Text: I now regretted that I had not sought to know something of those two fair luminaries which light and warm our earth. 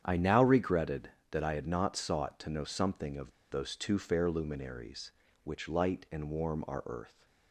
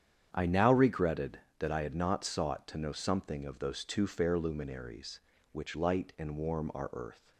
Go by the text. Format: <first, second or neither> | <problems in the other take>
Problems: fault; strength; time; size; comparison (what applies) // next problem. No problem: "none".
second | starts louder than the rest; strong; until 1.0 s; 8.5 dB; strong in the second // pauses between "of" and "those"; slight; at 3.2 s; 0.21 s long